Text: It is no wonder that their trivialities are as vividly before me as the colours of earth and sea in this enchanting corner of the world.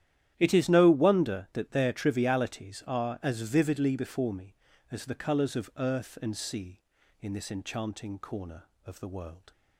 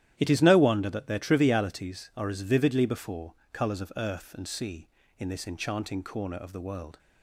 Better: first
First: starts louder than the rest; strong; until 1.3 s; 11.5 dB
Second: starts louder than the rest; strong; until 1.1 s; 12 dB // skips "me as the"; at 3.4 s

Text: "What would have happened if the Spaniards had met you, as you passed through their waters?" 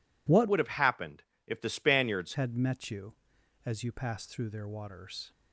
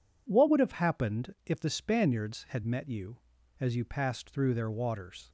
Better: second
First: changes voice from "would" to "Spaniards"; from 0.4 to 2.3 s; 1.9 s long // pauses between "happened" and "if"; slight; at 1.2 s; 0.24 s long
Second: none

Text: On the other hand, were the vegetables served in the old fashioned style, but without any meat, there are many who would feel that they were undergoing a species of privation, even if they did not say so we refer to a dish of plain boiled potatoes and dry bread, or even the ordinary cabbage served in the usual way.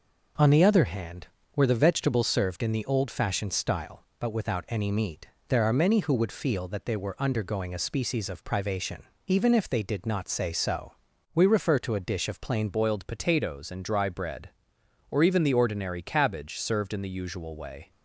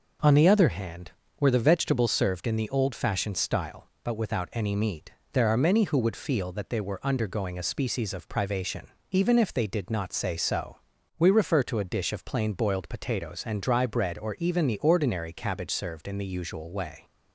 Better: second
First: pauses between "so" and "we"; at 10.9 s; 0.42 s long // changes voice at "boiled"; from 12.7 s on; 5.2 s long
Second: pauses between "so" and "we"; at 10.7 s; 0.42 s long

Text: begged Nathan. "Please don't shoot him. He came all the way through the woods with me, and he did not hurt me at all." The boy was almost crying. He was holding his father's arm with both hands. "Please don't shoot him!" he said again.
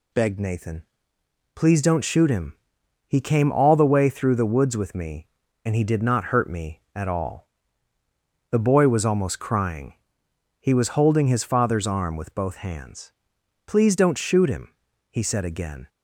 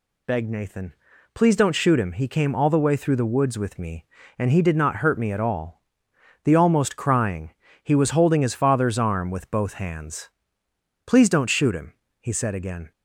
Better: first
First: none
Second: skips "boy was"; at 6.5 s

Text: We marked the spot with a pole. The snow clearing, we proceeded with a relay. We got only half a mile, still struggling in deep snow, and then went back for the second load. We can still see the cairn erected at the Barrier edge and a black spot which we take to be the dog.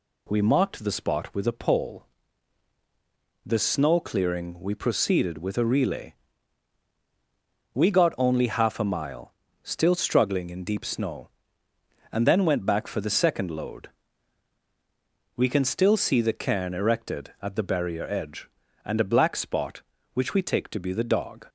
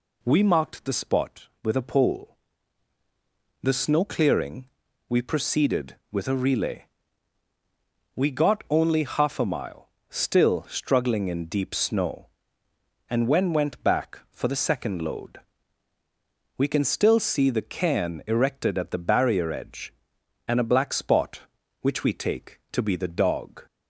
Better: first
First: none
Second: says "when" for "then"; at 13.2 s

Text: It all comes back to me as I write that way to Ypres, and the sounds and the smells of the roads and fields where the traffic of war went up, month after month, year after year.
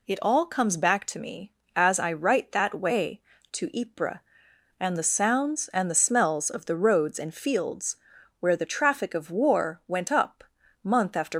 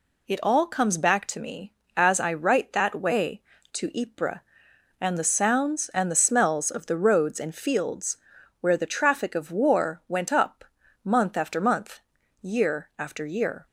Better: second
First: pauses between "fields" and "where"; at 7.9 s; 0.42 s long // stops before "month year after year"; at 11.3 s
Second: pauses between "fields" and "where"; at 8.1 s; 0.42 s long

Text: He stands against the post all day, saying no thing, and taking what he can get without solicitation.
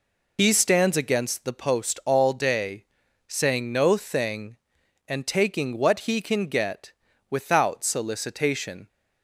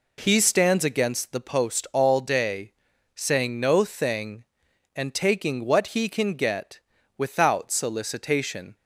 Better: second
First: loses the start of "He"; at 0.3 s; 85 ms // pauses between "get" and "without"; slight; at 6.9 s; 0.36 s long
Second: pauses between "get" and "without"; slight; at 6.8 s; 0.36 s long

